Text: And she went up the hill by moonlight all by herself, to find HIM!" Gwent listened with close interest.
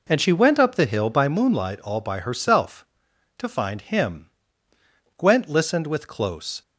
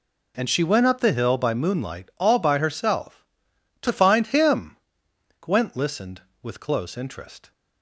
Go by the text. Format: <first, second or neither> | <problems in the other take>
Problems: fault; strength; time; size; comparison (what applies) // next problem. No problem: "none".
second | stops before "interest"; at 6.6 s